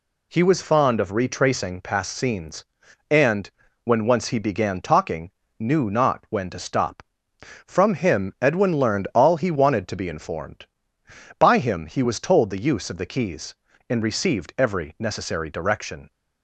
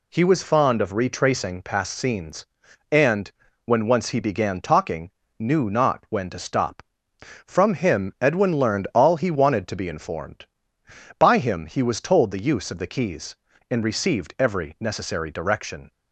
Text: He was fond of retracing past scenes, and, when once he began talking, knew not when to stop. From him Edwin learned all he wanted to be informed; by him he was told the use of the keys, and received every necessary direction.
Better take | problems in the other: neither | none

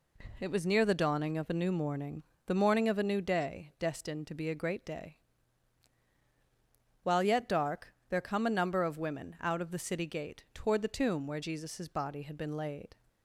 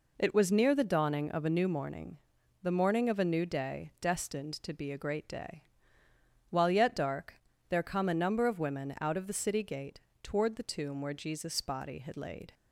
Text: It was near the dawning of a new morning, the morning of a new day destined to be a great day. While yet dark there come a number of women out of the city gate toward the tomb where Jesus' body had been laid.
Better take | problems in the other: first | pauses between "dark" and "there"; slight; at 7.3 s; 0.36 s long; slight in the first // pauses between "gate" and "toward"; slight; at 9.9 s; 0.24 s long // skips "been"; at 12.1 s

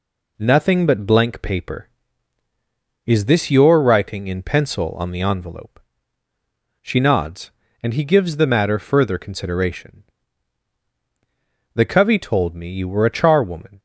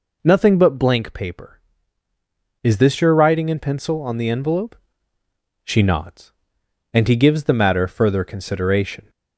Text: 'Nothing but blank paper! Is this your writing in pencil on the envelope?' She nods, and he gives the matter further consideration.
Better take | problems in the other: second | goes on to say "The covey told me you were a charwoman"; strong; from 11.7 s on; 2.0 s long

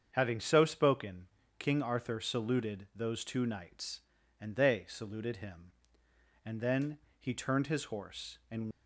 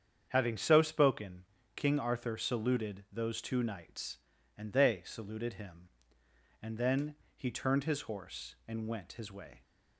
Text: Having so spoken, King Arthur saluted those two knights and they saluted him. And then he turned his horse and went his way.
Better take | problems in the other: second | starts louder than the rest; strong; until 1.1 s; 7.5 dB; strong in the second // pauses between "then" and "he"; slight; at 6.9 s; 0.22 s long; slight in the second // stops before "went his way"; at 8.7 s

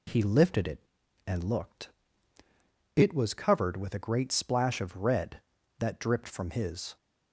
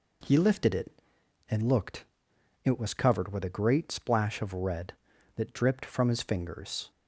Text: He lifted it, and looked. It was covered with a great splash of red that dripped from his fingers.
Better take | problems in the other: second | stops before "fingers"; at 6.9 s

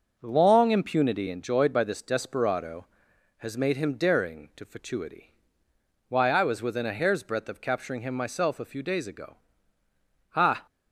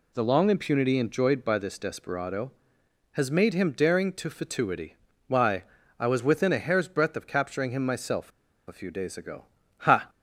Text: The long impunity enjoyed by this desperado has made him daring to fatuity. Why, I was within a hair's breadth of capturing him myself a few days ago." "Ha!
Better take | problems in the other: first | pauses between "myself" and "a"; at 8.3 s; 0.36 s long

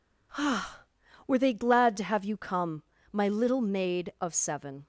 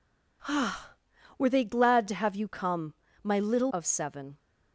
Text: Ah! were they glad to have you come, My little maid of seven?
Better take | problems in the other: first | skips "maid"; at 3.7 s

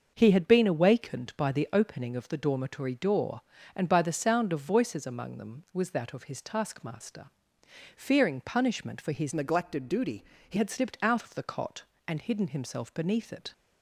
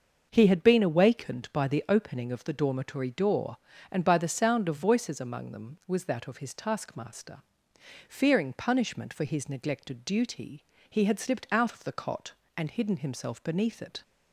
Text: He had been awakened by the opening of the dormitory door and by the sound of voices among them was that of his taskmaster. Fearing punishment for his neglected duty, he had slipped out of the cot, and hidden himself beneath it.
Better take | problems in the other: second | starts louder than the rest; until 1.1 s; 6.5 dB; also in the second // changes voice from "neglected" to "he"; from 9.3 to 10.5 s; 1.2 s long

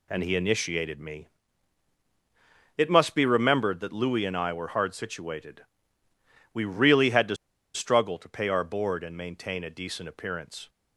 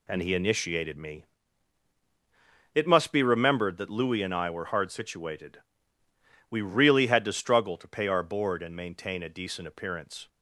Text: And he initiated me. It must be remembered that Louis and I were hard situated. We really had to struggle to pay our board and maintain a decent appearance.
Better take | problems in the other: second | pauses between "to" and "struggle"; at 7.3 s; 0.39 s long

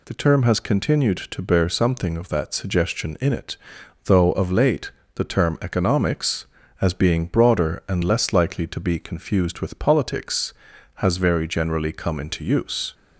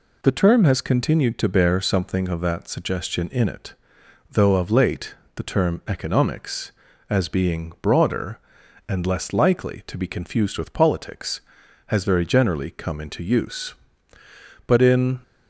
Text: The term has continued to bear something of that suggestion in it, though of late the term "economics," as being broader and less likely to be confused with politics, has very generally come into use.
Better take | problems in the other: first | pauses between "late" and "the"; slight; at 5.1 s; 0.20 s long; slight in the first // goes on to say "But in"; from 14.6 s on; 0.54 s long

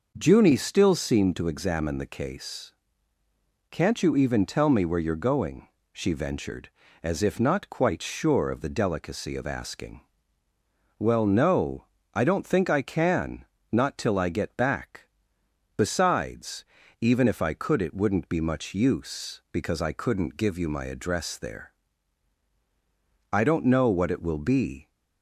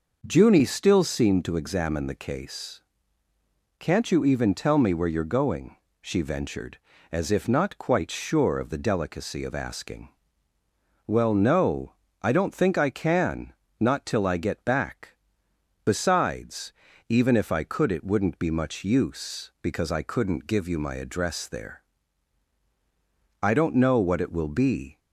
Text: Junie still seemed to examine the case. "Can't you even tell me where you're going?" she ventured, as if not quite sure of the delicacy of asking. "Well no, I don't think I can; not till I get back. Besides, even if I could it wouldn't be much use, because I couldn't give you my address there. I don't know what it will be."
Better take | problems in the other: neither | none

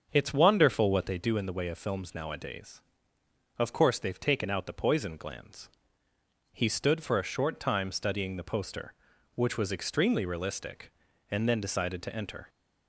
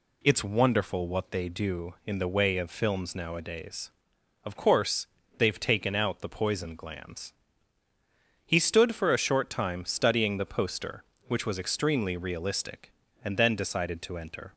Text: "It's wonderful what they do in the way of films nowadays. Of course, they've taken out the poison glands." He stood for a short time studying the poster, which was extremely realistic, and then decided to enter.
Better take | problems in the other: second | starts louder than the rest; until 1.1 s; 7 dB

